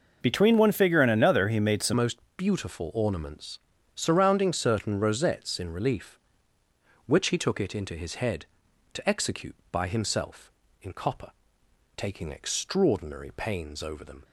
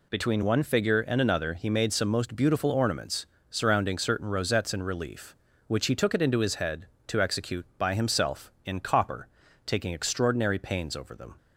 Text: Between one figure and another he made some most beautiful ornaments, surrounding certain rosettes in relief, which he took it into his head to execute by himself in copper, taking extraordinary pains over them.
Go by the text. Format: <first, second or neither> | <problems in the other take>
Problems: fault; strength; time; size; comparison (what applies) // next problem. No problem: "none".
second | changes voice at "most"; from 1.9 s on; 12.3 s long // pauses between "most" and "beautiful"; slight; at 2.2 s; 0.16 s long